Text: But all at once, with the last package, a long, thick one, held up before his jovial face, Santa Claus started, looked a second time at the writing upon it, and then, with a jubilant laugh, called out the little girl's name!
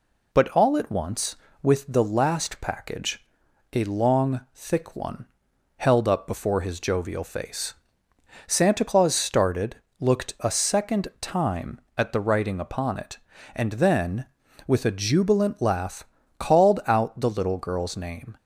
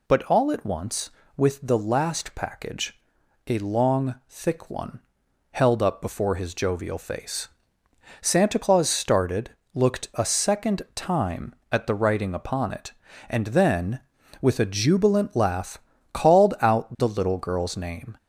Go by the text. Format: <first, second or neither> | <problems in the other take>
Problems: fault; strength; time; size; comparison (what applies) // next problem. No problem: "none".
first | gets louder; throughout; 3.5 dB